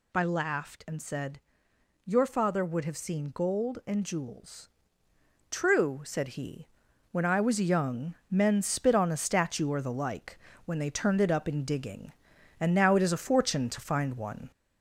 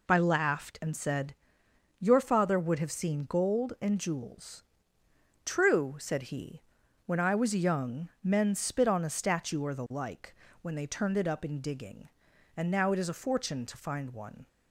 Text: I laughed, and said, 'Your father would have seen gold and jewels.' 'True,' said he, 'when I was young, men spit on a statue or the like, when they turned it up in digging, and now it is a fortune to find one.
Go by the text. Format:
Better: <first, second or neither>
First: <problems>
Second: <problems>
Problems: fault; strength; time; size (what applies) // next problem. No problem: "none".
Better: second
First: gets louder; slight; throughout; 2.5 dB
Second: none